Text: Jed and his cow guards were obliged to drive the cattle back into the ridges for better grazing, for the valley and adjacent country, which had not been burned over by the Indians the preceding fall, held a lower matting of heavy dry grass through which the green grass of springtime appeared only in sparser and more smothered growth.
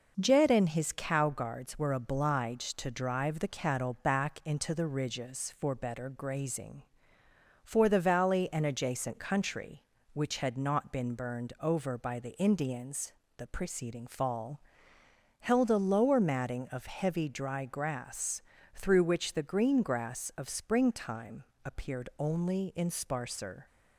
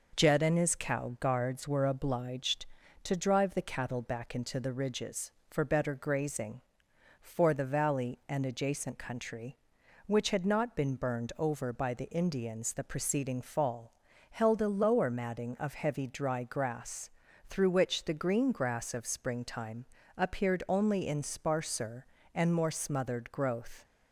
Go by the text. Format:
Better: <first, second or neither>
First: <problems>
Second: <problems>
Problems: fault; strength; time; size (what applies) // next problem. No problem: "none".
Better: second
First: pauses between "Indians" and "the"; slight; at 13.1 s; 0.24 s long // pauses between "grass" and "through"; slight; at 18.3 s; 0.34 s long // pauses between "springtime" and "appeared"; slight; at 21.4 s; 0.32 s long // stops before "and more smothered growth"; at 23.6 s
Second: pauses between "grass" and "through"; at 17.1 s; 0.38 s long // pauses between "springtime" and "appeared"; slight; at 19.8 s; 0.32 s long